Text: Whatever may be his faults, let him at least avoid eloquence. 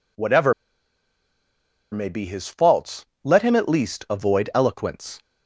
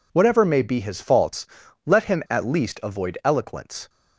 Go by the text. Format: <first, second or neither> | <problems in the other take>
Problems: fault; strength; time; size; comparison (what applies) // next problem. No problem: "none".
second | pauses between "Whatever" and "may"; strong; at 0.5 s; 1.3 s long